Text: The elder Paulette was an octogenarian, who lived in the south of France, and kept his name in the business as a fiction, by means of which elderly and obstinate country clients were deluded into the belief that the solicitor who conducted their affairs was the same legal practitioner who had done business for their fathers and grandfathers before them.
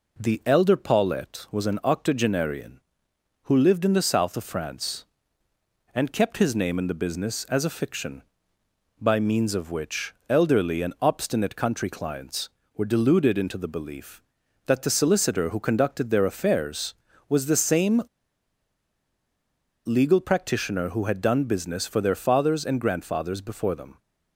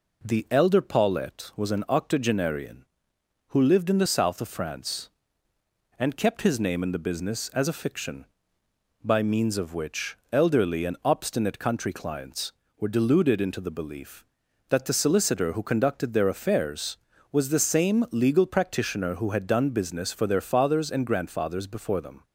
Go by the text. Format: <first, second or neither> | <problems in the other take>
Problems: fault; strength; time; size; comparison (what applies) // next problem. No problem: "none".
second | pauses between "same" and "legal"; strong; at 18.0 s; 1.8 s long